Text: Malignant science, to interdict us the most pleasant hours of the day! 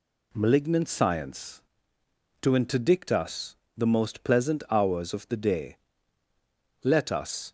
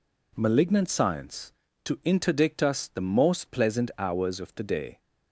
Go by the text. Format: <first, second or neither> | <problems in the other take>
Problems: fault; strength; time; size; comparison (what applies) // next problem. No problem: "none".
second | pauses between "us" and "the"; slight; at 3.5 s; 0.18 s long // goes on to say "Let us"; noticeable; from 6.8 s on; 0.66 s long